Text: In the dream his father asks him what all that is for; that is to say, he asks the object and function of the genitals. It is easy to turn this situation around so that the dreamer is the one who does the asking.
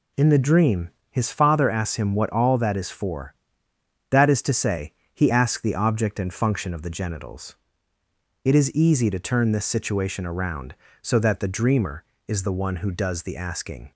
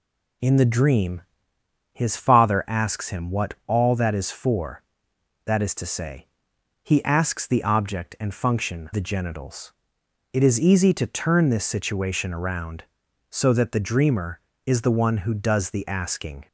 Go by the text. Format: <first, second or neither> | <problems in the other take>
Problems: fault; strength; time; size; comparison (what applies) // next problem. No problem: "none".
first | pauses between "dream" and "his"; noticeable; at 1.2 s; 0.70 s long; slight in the first // skips "of"; at 8.9 s